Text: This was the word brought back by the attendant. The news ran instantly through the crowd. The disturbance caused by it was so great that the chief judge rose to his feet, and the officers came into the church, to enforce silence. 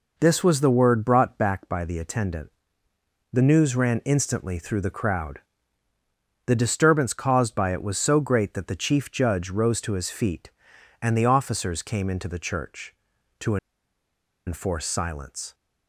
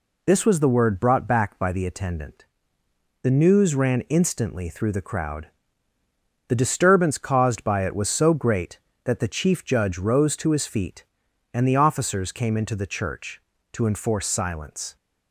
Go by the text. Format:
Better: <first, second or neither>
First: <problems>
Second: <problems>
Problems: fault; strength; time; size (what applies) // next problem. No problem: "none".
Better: second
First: pauses between "to" and "enforce"; noticeable; at 13.5 s; 0.90 s long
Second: none